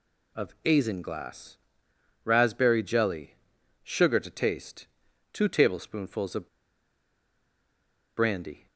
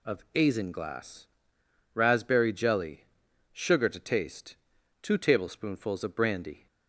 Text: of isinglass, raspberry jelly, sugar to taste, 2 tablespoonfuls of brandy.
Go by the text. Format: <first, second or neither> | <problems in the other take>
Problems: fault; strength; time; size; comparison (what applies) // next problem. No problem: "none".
second | pauses between "of" and "brandy"; strong; at 6.4 s; 1.7 s long